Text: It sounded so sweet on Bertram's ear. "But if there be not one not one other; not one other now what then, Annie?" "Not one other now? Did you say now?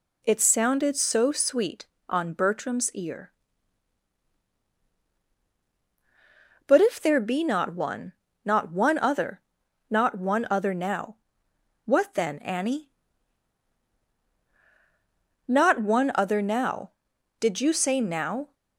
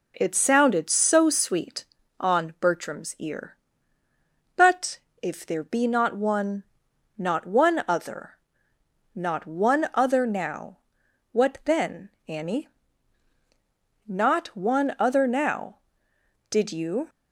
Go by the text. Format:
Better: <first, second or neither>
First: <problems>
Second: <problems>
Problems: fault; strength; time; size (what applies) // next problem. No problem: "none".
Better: first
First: pauses between "one" and "not"; slight; at 8.1 s; 0.32 s long // pauses between "now" and "what"; noticeable; at 11.1 s; 0.66 s long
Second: pauses between "But" and "if"; slight; at 4.9 s; 0.22 s long // pauses between "one" and "not"; noticeable; at 6.6 s; 0.54 s long // pauses between "now" and "what"; noticeable; at 10.7 s; 0.56 s long // stops before "say now"; at 17.0 s